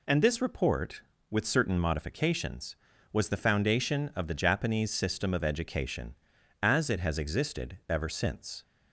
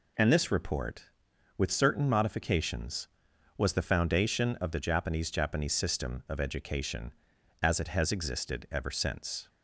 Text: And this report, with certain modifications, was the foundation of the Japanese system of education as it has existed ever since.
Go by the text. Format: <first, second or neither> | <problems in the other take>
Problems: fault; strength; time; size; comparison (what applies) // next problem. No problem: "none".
first | says "Japanese" twice; at 5.2 s